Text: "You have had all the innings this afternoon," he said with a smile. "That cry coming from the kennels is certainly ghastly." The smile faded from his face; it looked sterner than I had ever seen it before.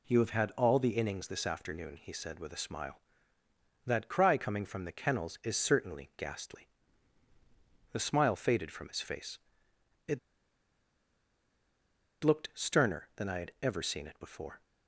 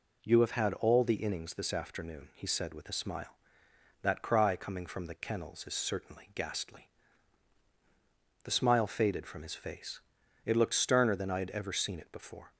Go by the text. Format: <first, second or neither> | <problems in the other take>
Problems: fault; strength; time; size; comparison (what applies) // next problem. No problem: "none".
second | pauses between "it" and "looked"; strong; at 10.1 s; 2.0 s long